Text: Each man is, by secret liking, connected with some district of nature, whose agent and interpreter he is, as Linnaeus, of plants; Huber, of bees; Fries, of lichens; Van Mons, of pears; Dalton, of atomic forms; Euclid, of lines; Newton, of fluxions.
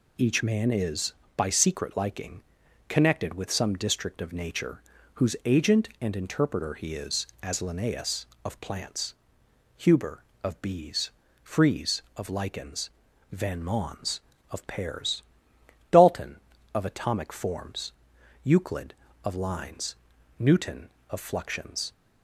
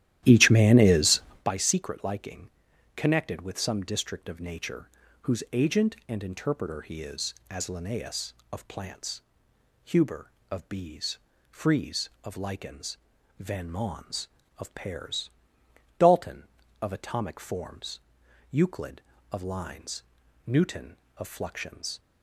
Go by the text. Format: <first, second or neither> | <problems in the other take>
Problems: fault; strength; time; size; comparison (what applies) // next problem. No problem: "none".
first | starts louder than the rest; strong; until 1.5 s; 13 dB